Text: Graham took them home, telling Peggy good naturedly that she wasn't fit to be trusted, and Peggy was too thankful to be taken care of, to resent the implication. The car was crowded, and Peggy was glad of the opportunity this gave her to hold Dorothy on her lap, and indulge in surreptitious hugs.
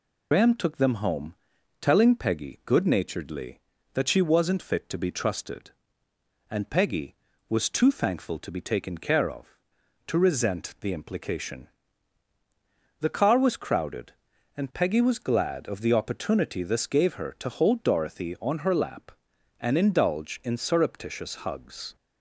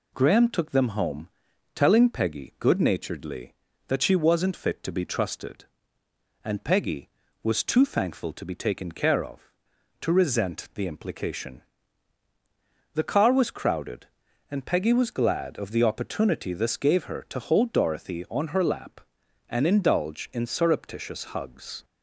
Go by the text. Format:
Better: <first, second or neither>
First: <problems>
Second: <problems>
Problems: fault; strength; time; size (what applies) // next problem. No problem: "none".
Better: second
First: loses the start of "Graham"; at 0.3 s; 105 ms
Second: none